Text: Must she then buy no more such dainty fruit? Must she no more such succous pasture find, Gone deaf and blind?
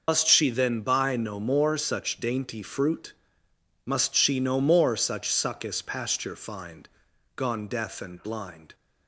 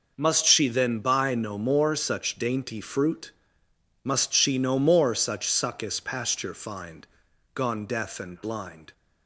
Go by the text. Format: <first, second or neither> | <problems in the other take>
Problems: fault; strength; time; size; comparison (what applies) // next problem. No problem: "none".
second | loses the start of "Must"; at 0.0 s; 100 ms